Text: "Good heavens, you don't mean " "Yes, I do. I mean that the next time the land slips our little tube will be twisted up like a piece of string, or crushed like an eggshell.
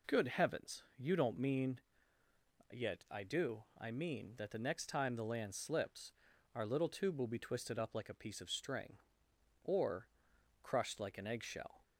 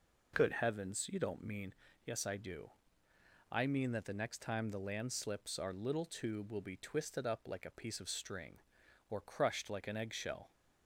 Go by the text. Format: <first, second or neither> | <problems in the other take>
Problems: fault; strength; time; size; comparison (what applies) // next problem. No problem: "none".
second | says "Yet" for "Yes"; at 2.7 s // pauses between "slips" and "our"; at 6.1 s; 0.42 s long // pauses between "or" and "crushed"; noticeable; at 10.0 s; 0.54 s long